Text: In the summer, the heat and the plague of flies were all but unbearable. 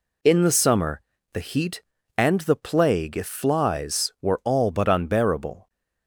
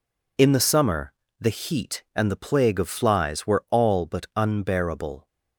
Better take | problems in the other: second | says "if" for "of"; at 3.1 s

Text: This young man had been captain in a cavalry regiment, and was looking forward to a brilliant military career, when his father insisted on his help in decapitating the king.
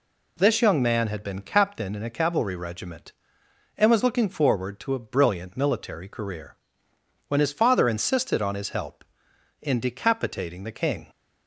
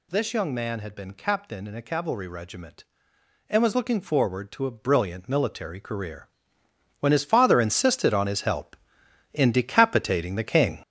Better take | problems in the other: first | gets louder; strong; throughout; 7.5 dB

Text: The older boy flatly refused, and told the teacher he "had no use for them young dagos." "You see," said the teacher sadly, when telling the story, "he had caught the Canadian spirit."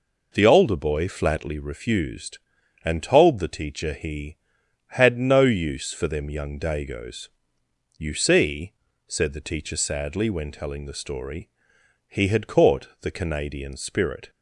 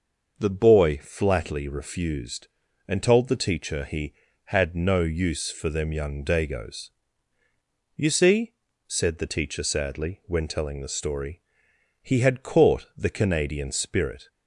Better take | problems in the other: first | starts louder than the rest; noticeable; until 1.3 s; 6 dB // skips "older"; at 0.4 s

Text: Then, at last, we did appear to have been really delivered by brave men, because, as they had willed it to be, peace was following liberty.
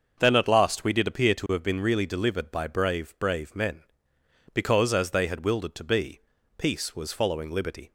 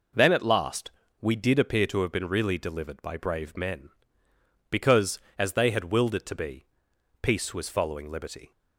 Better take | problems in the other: second | starts louder than the rest; until 1.2 s; 6.5 dB // says "brave" twice; at 3.1 s

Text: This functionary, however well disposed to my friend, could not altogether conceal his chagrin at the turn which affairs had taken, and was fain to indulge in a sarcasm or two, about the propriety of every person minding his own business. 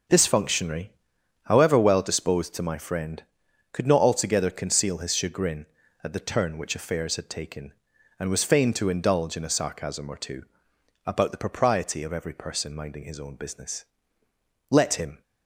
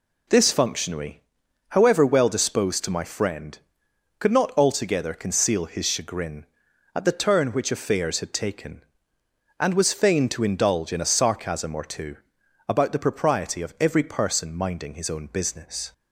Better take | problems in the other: second | goes on to say "Let him"; from 14.6 s on; 0.52 s long

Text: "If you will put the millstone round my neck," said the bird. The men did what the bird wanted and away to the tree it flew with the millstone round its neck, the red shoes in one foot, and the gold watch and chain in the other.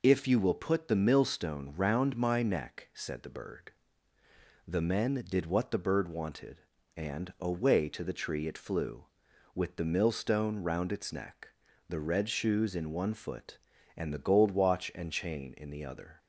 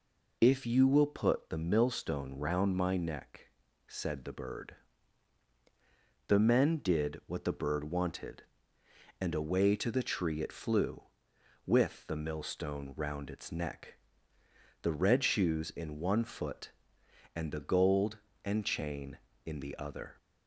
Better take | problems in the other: first | skips "watch"; at 18.3 s

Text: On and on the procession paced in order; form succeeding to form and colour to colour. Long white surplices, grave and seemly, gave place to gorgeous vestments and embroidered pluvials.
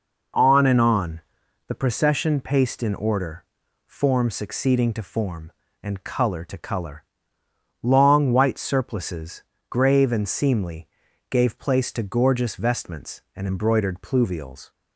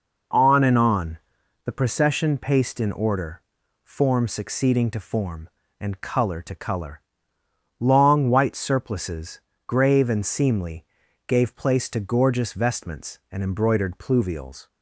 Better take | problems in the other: neither | pauses between "on" and "the"; noticeable; the same in both

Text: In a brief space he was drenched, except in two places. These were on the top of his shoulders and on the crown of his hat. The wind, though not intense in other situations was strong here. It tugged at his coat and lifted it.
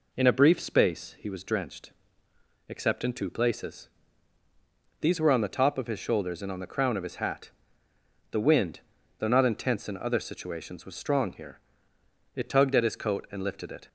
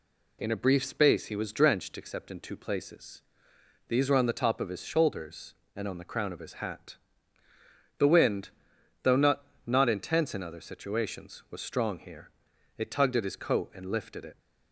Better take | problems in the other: first | says "not" twice; at 9.6 s

